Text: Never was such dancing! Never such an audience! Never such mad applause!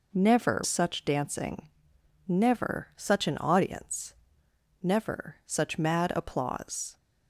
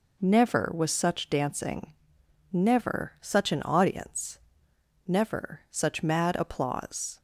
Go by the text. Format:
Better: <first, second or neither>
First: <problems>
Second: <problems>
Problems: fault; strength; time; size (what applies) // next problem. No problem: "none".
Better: second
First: skips "was"; at 0.6 s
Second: none